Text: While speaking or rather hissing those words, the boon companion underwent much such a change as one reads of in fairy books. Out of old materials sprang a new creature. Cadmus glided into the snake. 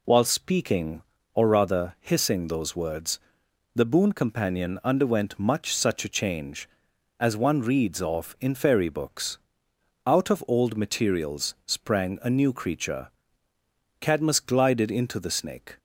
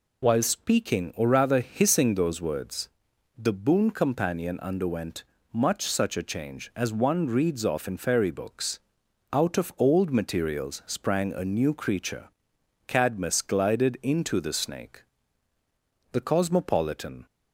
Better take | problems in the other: first | pauses between "underwent" and "much"; slight; at 5.2 s; 0.28 s long // goes on to say "The cosmopolitan"; noticeable; from 16.1 s on; 1.1 s long

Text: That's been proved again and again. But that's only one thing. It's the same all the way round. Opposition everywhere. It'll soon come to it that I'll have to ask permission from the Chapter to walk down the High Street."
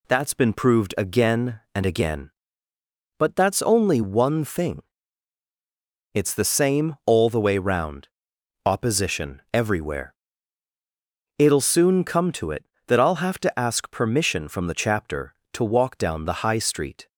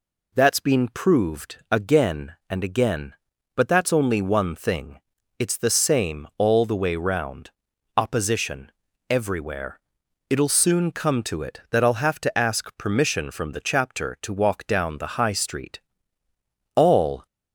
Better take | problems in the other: first | pauses between "Opposition" and "everywhere"; at 8.7 s; 0.40 s long // goes on to say "All"; from 16.7 s on; 0.50 s long

